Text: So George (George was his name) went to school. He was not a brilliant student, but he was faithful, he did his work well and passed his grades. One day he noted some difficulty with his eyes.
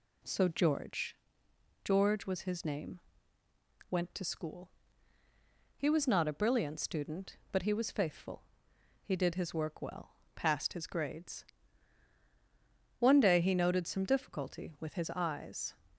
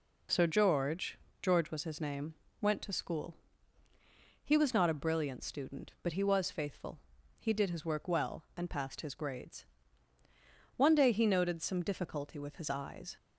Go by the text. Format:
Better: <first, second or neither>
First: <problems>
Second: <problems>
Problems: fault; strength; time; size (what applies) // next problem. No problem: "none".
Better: second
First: skips "and"; at 10.2 s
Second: none